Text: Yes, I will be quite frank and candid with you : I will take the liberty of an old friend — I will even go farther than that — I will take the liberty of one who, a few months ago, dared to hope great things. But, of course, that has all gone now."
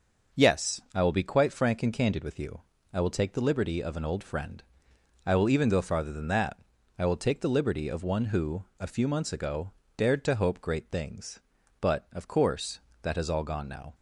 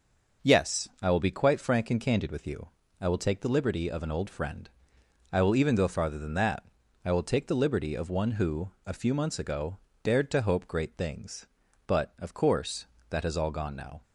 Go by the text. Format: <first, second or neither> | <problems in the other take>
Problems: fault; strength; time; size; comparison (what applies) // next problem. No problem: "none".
neither | starts louder than the rest; noticeable; the same in both